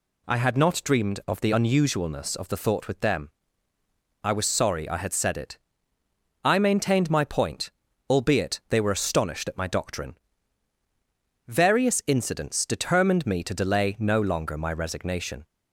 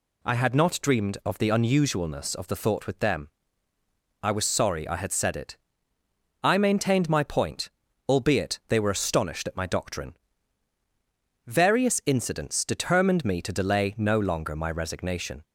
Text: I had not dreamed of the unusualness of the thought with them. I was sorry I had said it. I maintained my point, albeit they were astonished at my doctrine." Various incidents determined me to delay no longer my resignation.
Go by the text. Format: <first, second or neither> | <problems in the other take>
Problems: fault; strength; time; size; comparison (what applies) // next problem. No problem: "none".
neither | none